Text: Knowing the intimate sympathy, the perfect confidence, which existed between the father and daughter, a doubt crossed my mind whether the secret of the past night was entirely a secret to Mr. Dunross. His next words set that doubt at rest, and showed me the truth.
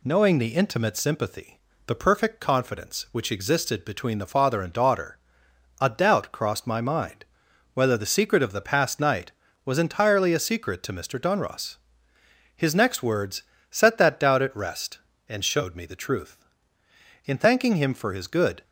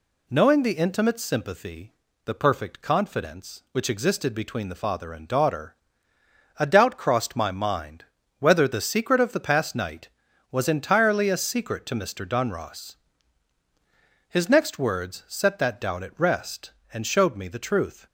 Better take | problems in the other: second | pauses between "mind" and "whether"; noticeable; at 7.2 s; 0.48 s long; slight in the second // pauses between "words" and "set"; slight; at 13.4 s; 0.26 s long // goes on to say "In thanking him for his good"; from 17.2 s on; 1.3 s long

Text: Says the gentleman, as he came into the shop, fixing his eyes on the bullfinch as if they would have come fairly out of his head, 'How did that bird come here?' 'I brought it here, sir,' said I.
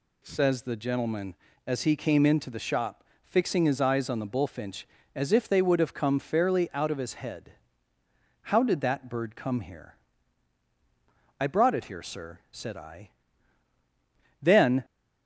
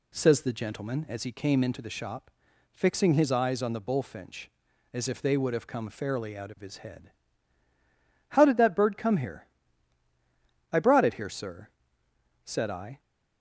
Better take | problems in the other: second | goes on to say "Then"; slight; from 14.4 s on; 0.42 s long

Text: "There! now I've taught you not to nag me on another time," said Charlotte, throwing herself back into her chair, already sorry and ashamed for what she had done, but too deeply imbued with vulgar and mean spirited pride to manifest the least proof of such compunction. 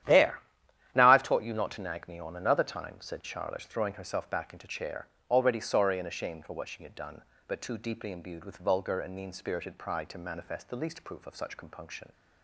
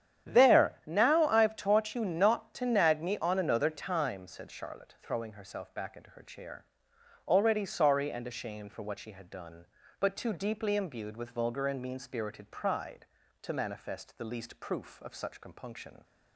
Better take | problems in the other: second | starts louder than the rest; strong; until 1.5 s; 11 dB; strong in the second // skips "her"; at 4.6 s

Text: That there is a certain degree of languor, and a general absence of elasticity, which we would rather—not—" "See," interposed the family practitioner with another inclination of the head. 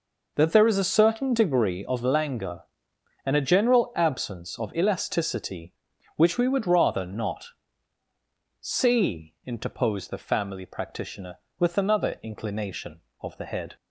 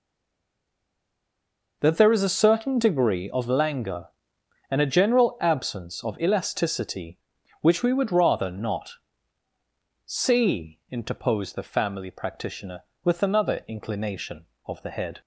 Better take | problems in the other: first | stays silent before the first word; noticeable; until 1.8 s; 1.8 s long

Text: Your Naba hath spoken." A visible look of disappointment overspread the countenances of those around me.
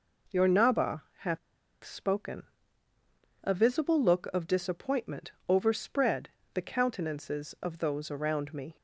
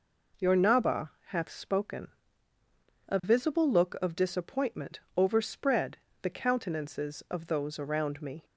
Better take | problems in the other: second | pauses between "Naba" and "hath"; slight; at 1.0 s; 0.16 s long; slight in the second // pauses between "hath" and "spoken"; at 1.3 s; 0.45 s long // pauses between "disappointment" and "overspread"; slight; at 5.3 s; 0.16 s long; slight in the second // pauses between "overspread" and "the"; slight; at 6.2 s; 0.26 s long; slight in the second

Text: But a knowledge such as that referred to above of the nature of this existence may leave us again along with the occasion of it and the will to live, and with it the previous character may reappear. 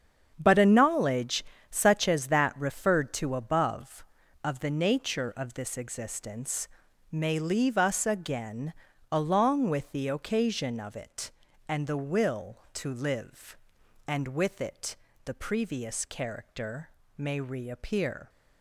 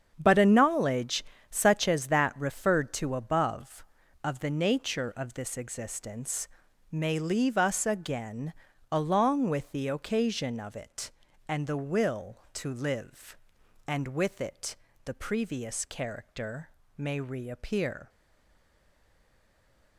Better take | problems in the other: first | starts louder than the rest; strong; until 1.1 s; 8 dB; strong in the first // pauses between "knowledge" and "such"; slight; at 1.2 s; 0.26 s long; slight in the first // pauses between "existence" and "may"; at 6.4 s; 0.44 s long; also in the first // pauses between "again" and "along"; at 8.5 s; 0.38 s long; also in the first // pauses between "it" and "the"; slight; at 14.7 s; 0.28 s long; slight in the first // pauses between "character" and "may"; slight; at 16.6 s; 0.28 s long; slight in the first // stays silent after the last word; noticeable; from 18.0 s on; 1.9 s long

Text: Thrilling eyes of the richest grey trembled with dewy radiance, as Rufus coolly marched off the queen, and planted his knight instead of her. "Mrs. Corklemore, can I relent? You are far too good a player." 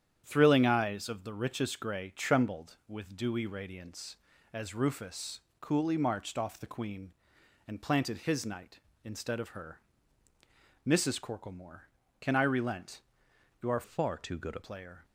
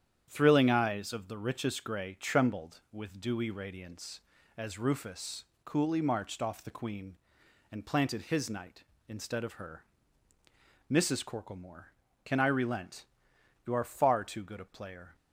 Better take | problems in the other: second | starts louder than the rest; strong; until 1.2 s; 9.5 dB; strong in the second // pauses between "Rufus" and "coolly"; slight; at 5.3 s; 0.20 s long; slight in the second // changes voice from "far" to "a"; from 13.8 to 14.6 s; 0.8 s long

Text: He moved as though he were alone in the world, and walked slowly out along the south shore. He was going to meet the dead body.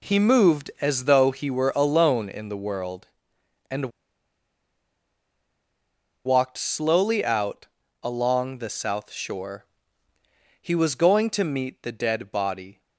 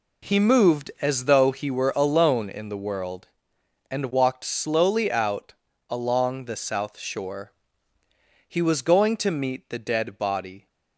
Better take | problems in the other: second | pauses between "and" and "walked"; strong; at 3.8 s; 2.3 s long // pauses between "out" and "along"; at 7.6 s; 0.38 s long; also in the second

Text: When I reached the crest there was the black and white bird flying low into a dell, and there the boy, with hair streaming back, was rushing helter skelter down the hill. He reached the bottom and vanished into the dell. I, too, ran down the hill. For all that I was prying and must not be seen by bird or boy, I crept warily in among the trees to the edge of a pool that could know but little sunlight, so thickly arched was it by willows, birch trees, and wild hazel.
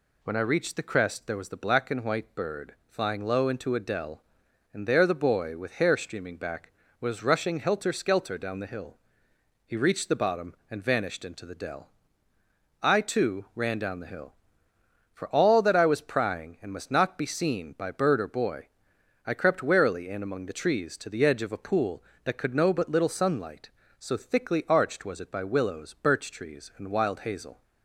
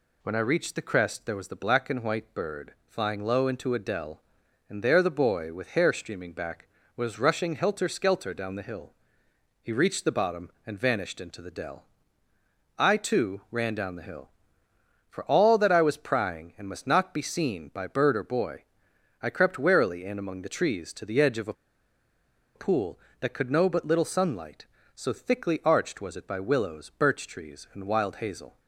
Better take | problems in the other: first | pauses between "a" and "pool"; at 21.5 s; 1.0 s long

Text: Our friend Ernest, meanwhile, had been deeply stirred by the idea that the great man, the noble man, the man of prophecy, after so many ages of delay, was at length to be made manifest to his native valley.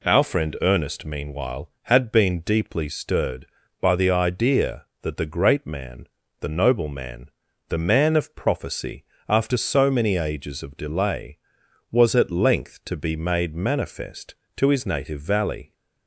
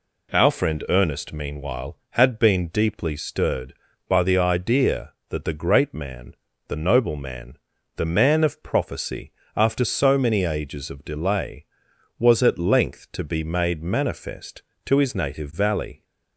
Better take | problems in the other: neither | none

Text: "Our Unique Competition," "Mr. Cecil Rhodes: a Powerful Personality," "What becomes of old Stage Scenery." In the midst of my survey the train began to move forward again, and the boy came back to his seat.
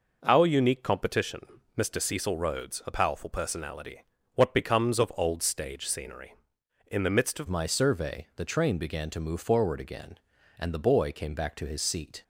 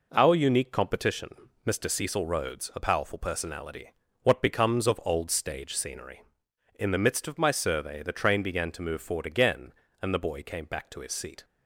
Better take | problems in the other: second | changes voice at "my"; from 7.4 s on; 4.8 s long

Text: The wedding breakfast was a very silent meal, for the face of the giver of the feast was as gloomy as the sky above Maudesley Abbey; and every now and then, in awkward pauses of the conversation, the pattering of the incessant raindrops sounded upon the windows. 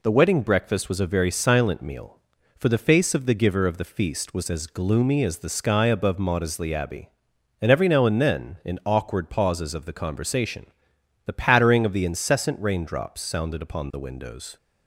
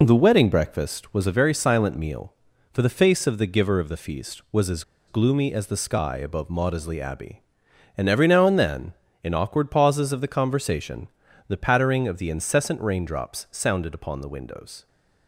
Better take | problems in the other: first | pauses between "as" and "gloomy"; slight; at 4.8 s; 0.25 s long

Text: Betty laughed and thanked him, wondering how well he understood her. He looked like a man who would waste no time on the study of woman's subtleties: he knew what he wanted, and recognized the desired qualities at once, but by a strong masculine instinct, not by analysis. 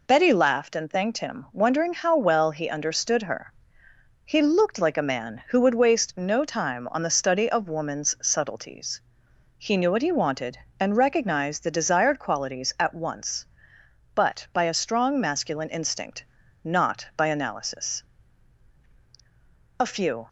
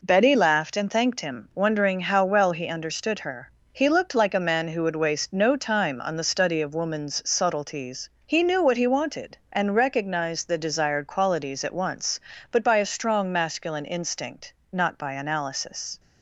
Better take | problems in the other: second | goes on to say "A few"; from 19.7 s on; 0.50 s long

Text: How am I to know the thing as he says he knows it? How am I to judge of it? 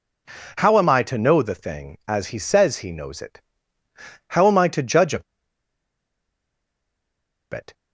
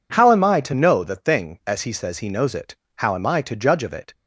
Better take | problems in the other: second | pauses between "of" and "it"; strong; at 5.2 s; 2.2 s long

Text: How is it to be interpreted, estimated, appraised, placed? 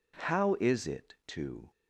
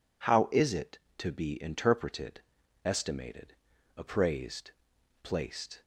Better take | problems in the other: second | stops before "be interpreted estimated appraised placed"; at 1.7 s

